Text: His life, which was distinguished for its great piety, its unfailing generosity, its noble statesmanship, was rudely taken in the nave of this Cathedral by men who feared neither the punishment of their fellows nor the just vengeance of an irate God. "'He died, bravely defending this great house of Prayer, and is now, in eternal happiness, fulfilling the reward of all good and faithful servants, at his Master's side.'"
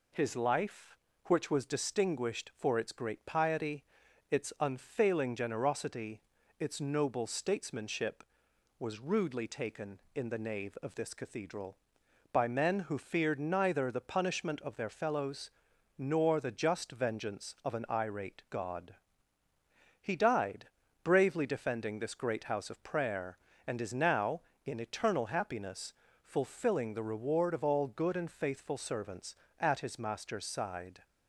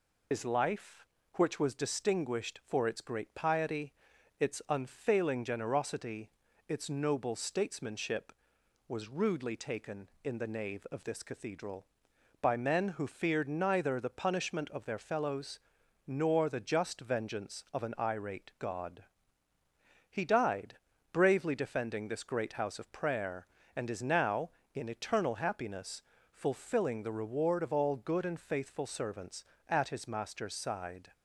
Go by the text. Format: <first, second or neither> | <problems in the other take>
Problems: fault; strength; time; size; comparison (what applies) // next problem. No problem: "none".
first | loses the start of "His"; at 0.3 s; 85 ms // pauses between "fellows" and "nor"; noticeable; at 15.5 s; 0.48 s long; noticeable in the first